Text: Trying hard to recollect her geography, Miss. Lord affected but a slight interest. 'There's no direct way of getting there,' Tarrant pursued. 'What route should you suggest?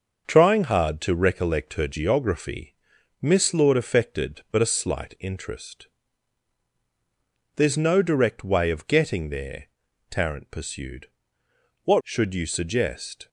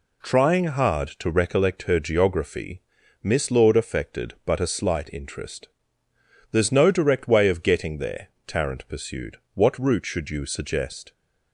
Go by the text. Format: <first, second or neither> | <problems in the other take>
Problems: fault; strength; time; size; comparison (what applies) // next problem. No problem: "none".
second | starts louder than the rest; until 1.2 s; 6 dB // skips "route"; at 12.0 s